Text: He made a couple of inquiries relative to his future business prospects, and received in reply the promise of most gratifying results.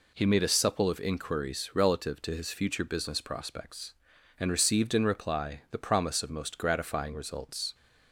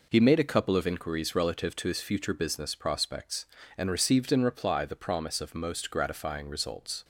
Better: second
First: says "supple" for "couple"; at 0.4 s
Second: none

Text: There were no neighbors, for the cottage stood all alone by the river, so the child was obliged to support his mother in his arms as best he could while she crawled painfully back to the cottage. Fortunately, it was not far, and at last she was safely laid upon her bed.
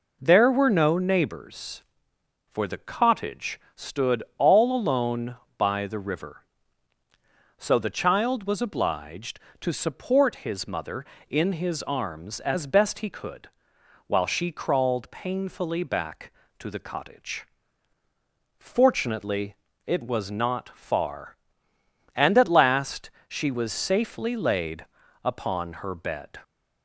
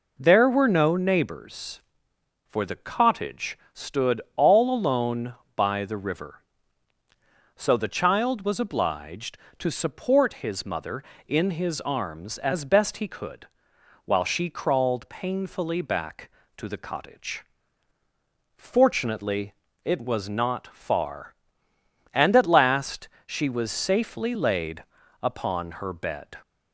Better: neither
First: pauses between "cottage" and "stood"; slight; at 3.6 s; 0.16 s long // pauses between "stood" and "all"; slight; at 4.2 s; 0.16 s long // pauses between "could" and "while"; noticeable; at 13.4 s; 0.60 s long // pauses between "last" and "she"; slight; at 23.0 s; 0.20 s long // pauses between "laid" and "upon"; at 24.8 s; 0.40 s long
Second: pauses between "cottage" and "stood"; slight; at 3.5 s; 0.16 s long // pauses between "stood" and "all"; slight; at 4.1 s; 0.16 s long // pauses between "could" and "while"; noticeable; at 13.4 s; 0.60 s long // pauses between "last" and "she"; slight; at 23.0 s; 0.20 s long // pauses between "laid" and "upon"; at 24.8 s; 0.40 s long

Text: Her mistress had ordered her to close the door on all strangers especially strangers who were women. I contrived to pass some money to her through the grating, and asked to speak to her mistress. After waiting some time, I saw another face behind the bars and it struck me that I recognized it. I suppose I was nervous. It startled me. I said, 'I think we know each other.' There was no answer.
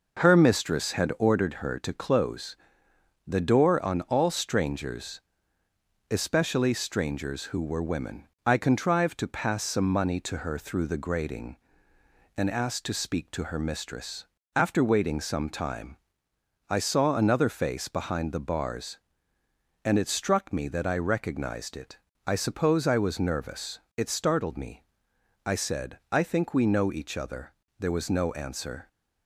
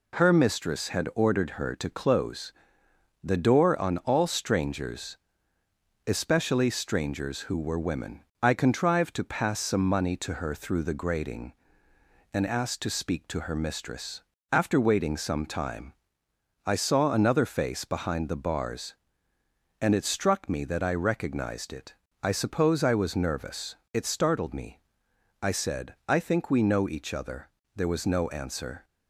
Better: second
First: starts louder than the rest; noticeable; until 1.5 s; 5.5 dB // pauses between "close" and "the"; noticeable; at 2.5 s; 0.72 s long // pauses between "strangers" and "especially"; noticeable; at 5.1 s; 0.90 s long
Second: pauses between "close" and "the"; noticeable; at 2.5 s; 0.72 s long // pauses between "strangers" and "especially"; noticeable; at 5.1 s; 0.90 s long

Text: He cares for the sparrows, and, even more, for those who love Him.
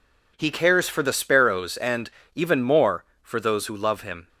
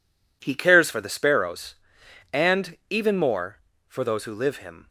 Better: first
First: none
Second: says "live" for "love"; at 4.3 s

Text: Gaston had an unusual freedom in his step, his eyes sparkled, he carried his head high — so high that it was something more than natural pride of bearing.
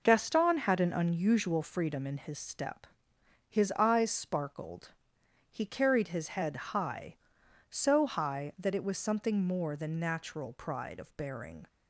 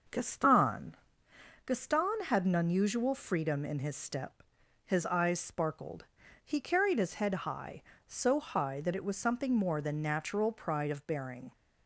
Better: first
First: none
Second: says "Gaston" twice; at 1.6 s

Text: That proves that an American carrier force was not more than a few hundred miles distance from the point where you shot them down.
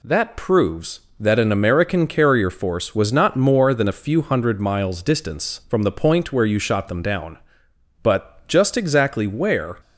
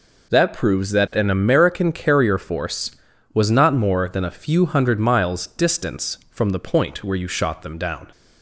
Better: second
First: goes on to say "But just exactly where"; strong; from 8.0 s on; 1.7 s long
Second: none

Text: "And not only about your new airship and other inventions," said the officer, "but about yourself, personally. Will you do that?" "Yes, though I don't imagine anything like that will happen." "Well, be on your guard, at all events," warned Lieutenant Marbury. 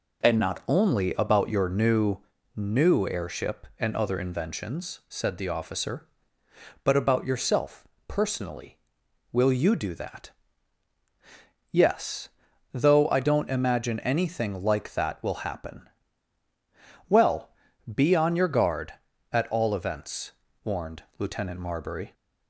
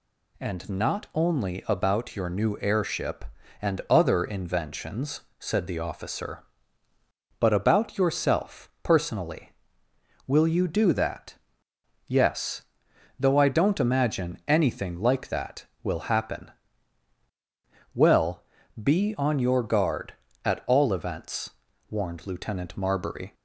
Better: second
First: says "new" twice; at 2.5 s // pauses between "warned" and "Lieutenant"; slight; at 21.0 s; 0.16 s long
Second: none

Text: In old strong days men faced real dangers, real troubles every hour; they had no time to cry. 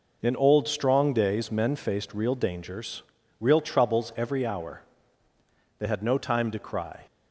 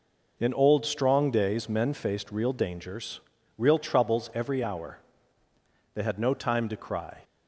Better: neither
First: none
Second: none

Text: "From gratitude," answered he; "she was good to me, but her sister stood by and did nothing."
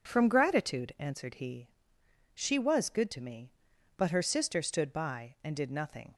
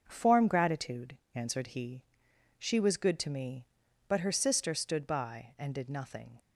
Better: first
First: none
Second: starts louder than the rest; until 1.0 s; 6.5 dB // says "Form" for "From"; at 0.0 s

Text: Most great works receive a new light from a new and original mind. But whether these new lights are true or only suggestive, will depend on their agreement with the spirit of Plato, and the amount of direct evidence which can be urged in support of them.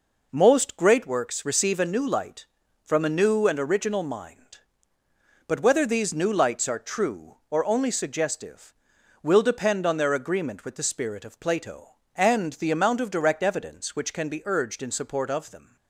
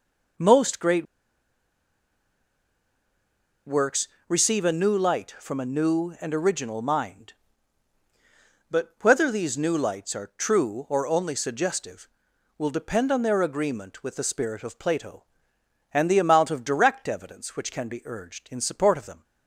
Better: first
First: none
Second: pauses between "great" and "works"; strong; at 1.0 s; 2.6 s long // pauses between "works" and "receive"; slight; at 4.0 s; 0.20 s long

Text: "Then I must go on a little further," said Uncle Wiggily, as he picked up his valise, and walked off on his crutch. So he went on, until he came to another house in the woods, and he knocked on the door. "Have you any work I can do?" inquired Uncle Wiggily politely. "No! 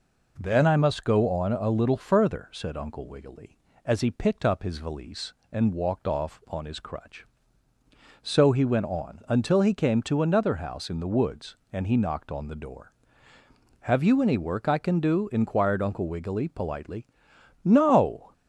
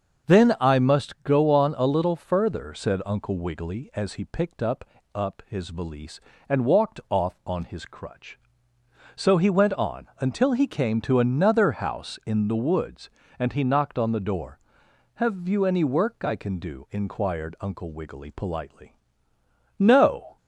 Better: first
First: none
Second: starts louder than the rest; until 1.3 s; 6.5 dB // says "up" twice; at 5.1 s

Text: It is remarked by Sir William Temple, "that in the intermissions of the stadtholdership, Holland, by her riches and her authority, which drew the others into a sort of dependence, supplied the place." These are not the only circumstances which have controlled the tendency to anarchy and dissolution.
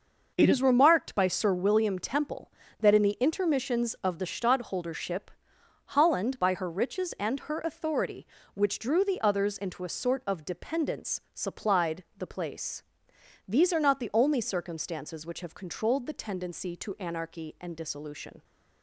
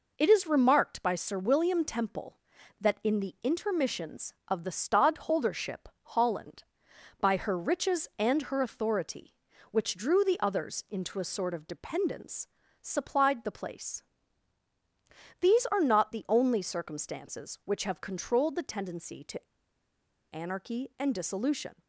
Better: first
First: none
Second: pauses between "to" and "anarchy"; noticeable; at 19.4 s; 0.88 s long

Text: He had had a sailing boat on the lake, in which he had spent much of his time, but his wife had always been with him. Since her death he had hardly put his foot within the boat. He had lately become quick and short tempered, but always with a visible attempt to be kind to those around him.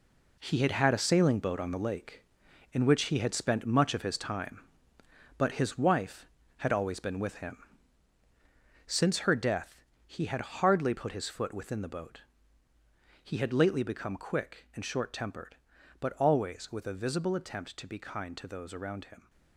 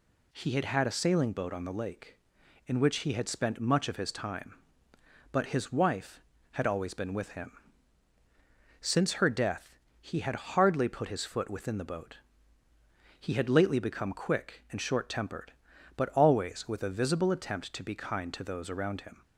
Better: second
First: gets quieter; strong; throughout; 9 dB // pauses between "death" and "he"; slight; at 9.8 s; 0.22 s long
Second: pauses between "death" and "he"; slight; at 9.7 s; 0.22 s long

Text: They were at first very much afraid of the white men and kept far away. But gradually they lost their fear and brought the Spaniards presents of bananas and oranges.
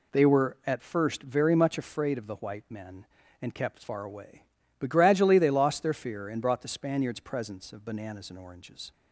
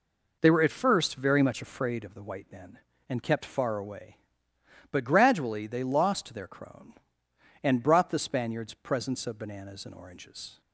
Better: first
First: none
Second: says "crone" for "fear"; at 6.4 s

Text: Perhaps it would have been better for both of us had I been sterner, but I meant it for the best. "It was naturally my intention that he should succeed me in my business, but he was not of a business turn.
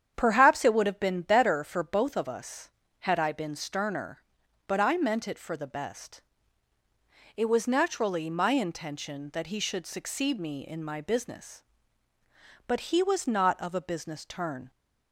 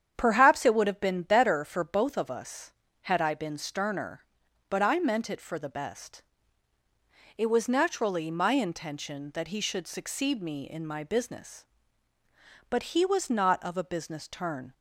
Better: neither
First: starts louder than the rest; strong; until 1.1 s; 8.5 dB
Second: starts louder than the rest; strong; until 1.1 s; 8.5 dB

